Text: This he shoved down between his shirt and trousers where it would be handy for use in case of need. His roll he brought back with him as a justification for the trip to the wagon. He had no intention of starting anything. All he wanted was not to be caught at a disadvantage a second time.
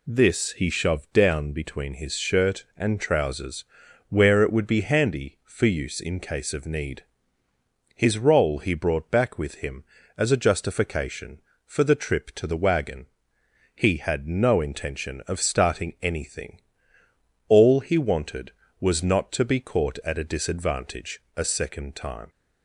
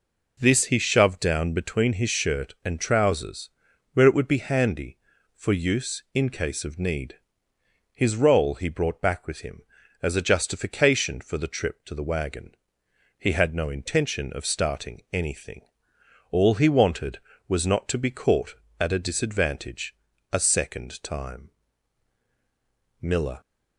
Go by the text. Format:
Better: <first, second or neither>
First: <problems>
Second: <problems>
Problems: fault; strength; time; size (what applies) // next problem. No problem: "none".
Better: first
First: pauses between "trousers" and "where"; at 3.6 s; 0.42 s long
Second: pauses between "trousers" and "where"; at 3.5 s; 0.44 s long // pauses between "disadvantage" and "a"; slight; at 19.9 s; 0.36 s long // goes on to say "Miller"; slight; from 23.0 s on; 0.40 s long